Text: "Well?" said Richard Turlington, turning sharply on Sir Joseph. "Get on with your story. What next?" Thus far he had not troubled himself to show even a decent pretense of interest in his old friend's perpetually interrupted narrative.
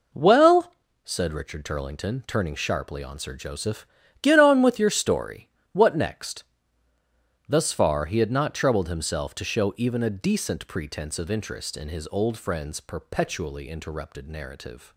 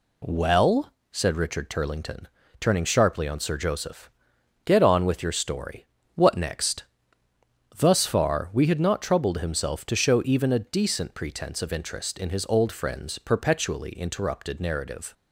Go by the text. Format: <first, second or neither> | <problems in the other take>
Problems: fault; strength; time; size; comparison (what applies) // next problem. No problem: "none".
first | says "we" for "he"; at 8.5 s